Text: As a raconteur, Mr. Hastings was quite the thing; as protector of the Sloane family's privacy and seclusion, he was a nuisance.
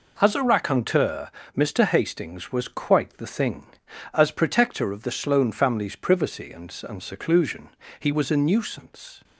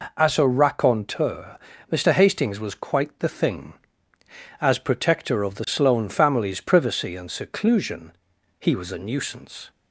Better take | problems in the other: second | says "and" twice; at 6.8 s

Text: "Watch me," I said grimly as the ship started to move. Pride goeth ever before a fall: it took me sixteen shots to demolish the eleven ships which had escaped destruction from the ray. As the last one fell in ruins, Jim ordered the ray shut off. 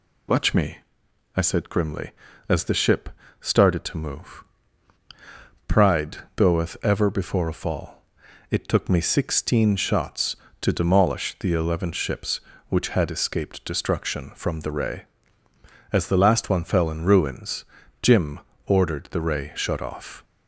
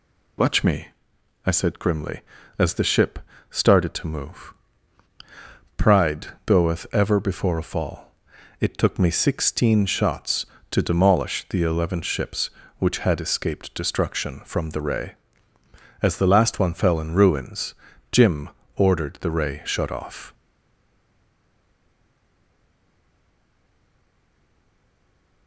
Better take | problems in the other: first | pauses between "ship" and "started"; slight; at 3.1 s; 0.30 s long; slight in the first // pauses between "Pride" and "goeth"; slight; at 6.2 s; 0.18 s long; slight in the first // pauses between "Jim" and "ordered"; slight; at 18.4 s; 0.30 s long; slight in the first // stays silent after the last word; strong; from 20.3 s on; 5.1 s long

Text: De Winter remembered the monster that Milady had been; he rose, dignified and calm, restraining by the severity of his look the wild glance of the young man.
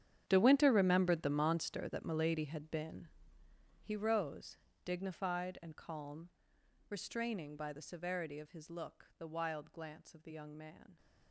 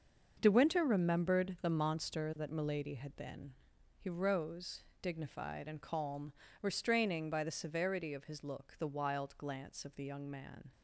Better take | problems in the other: second | gets quieter; strong; throughout; 17.5 dB // starts louder than the rest; strong; until 1.2 s; 10 dB; also in the second

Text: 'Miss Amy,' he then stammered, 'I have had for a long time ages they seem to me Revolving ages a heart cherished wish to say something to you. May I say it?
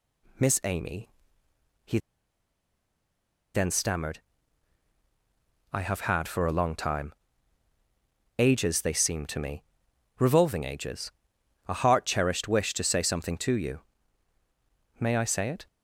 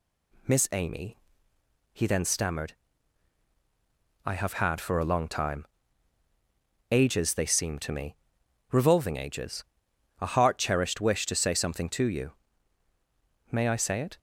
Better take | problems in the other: second | pauses between "he" and "then"; strong; at 1.9 s; 1.5 s long // pauses between "time" and "ages"; strong; at 7.1 s; 1.2 s long; strong in the second // pauses between "me" and "Revolving"; noticeable; at 9.6 s; 0.56 s long; noticeable in the second // pauses between "ages" and "a"; noticeable; at 11.1 s; 0.58 s long; noticeable in the second

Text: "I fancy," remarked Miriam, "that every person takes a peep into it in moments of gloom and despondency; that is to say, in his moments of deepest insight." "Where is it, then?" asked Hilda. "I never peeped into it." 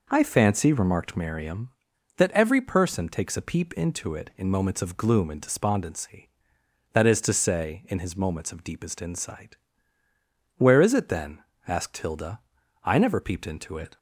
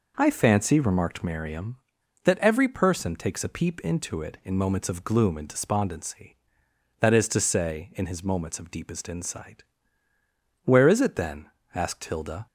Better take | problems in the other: first | stops before "I never peeped into it"; at 12.4 s

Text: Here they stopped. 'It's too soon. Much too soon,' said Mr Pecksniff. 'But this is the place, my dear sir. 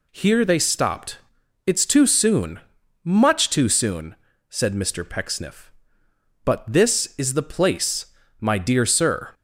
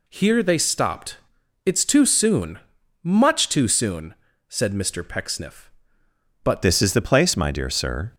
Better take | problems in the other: first | changes voice at "this"; from 6.6 s on; 1.5 s long

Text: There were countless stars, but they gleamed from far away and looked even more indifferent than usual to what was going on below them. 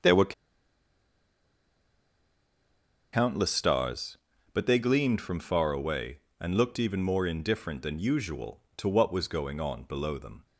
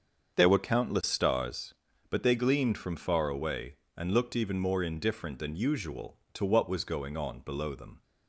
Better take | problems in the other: second | starts louder than the rest; until 3.8 s; 7 dB; also in the second // pauses between "were" and "countless"; strong; at 0.3 s; 2.8 s long

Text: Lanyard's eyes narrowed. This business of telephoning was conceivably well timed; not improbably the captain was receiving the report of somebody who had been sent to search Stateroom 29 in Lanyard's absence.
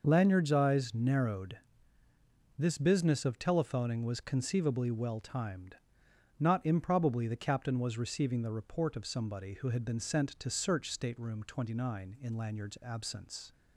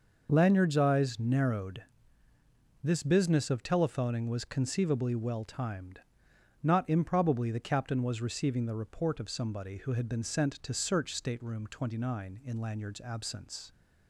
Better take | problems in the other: neither | none

